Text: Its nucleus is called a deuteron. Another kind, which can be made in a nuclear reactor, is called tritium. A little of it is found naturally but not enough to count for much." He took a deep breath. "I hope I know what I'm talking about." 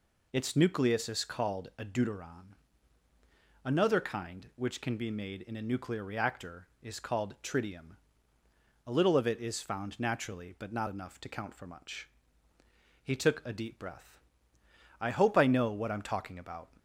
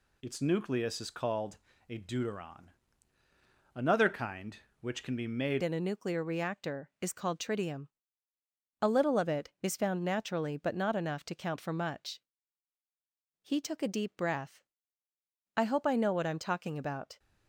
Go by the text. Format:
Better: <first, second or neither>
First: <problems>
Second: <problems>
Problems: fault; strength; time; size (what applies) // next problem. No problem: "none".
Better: first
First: none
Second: pauses between "called" and "a"; slight; at 1.5 s; 0.30 s long // changes voice at "in"; from 5.6 s on; 11.5 s long